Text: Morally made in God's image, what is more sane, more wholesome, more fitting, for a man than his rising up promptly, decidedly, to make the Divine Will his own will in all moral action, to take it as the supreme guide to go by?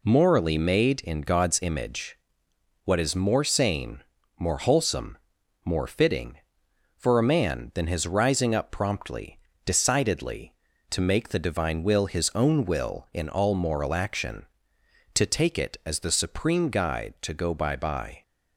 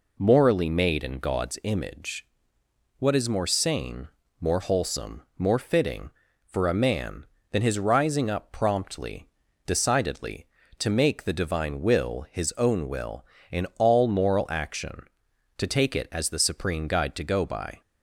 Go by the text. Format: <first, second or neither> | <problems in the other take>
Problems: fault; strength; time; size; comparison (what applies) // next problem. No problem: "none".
second | says "by" twice; at 17.7 s